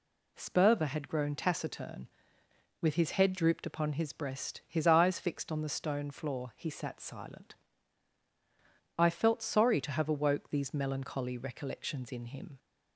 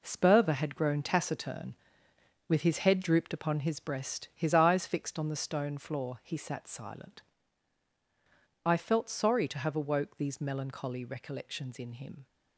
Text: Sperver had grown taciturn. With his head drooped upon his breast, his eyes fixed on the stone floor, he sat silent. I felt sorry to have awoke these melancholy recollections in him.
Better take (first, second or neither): first